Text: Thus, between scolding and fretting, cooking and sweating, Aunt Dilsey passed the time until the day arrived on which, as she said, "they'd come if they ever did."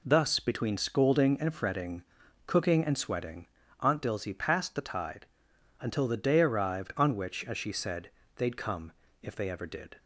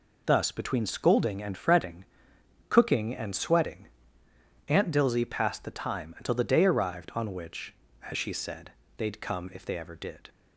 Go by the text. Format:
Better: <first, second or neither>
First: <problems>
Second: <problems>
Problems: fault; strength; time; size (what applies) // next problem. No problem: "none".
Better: second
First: says "tide" for "time"; at 4.8 s // pauses between "come" and "if"; slight; at 8.9 s; 0.30 s long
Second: none